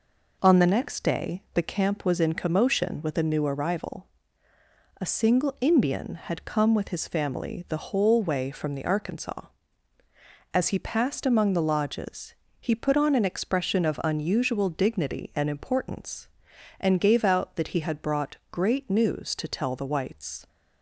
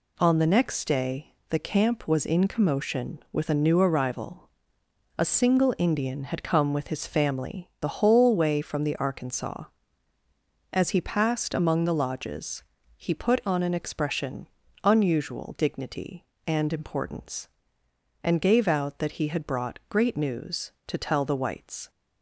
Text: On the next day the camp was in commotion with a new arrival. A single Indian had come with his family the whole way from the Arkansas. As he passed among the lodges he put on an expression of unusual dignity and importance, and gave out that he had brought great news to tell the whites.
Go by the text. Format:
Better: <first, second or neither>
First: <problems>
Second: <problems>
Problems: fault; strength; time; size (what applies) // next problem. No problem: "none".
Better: first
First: pauses between "lodges" and "he"; slight; at 12.3 s; 0.26 s long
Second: pauses between "day" and "the"; slight; at 1.3 s; 0.16 s long // pauses between "lodges" and "he"; slight; at 12.6 s; 0.32 s long // skips "of"; at 14.6 s